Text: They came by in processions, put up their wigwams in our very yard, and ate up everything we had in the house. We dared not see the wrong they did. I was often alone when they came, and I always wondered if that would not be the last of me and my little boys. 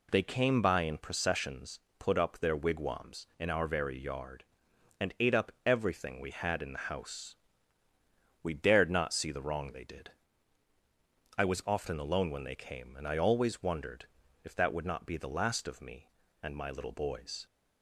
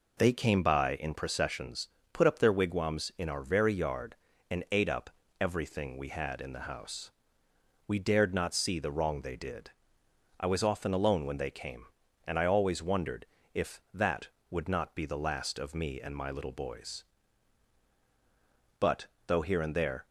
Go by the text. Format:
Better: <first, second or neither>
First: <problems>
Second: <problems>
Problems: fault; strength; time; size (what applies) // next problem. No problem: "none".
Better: first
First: pauses between "wondered" and "if"; at 14.0 s; 0.38 s long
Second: pauses between "up" and "everything"; slight; at 5.1 s; 0.30 s long // pauses between "wondered" and "if"; slight; at 13.2 s; 0.28 s long // goes on to say "But though here and there"; noticeable; from 18.8 s on; 1.2 s long